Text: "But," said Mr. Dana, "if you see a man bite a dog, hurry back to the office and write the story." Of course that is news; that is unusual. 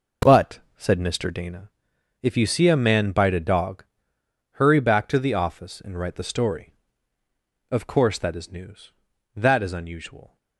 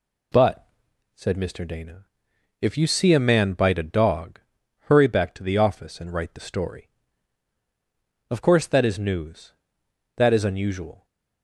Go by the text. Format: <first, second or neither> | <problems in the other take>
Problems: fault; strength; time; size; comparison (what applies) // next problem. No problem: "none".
second | starts louder than the rest; noticeable; until 1.7 s; 5 dB